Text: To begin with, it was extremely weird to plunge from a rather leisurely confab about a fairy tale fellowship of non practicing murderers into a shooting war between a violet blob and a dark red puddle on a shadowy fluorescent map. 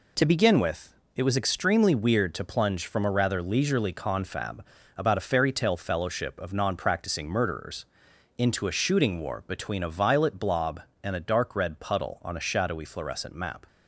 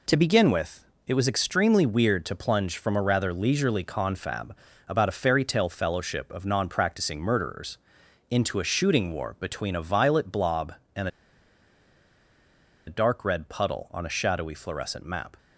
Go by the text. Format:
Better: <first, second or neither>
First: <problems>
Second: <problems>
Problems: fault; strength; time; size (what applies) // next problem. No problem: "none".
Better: first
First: pauses between "confab" and "about"; slight; at 4.6 s; 0.32 s long // pauses between "murderers" and "into"; noticeable; at 7.8 s; 0.50 s long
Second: pauses between "confab" and "about"; slight; at 4.5 s; 0.32 s long // pauses between "murderers" and "into"; noticeable; at 7.7 s; 0.50 s long // pauses between "and" and "a"; strong; at 11.0 s; 1.7 s long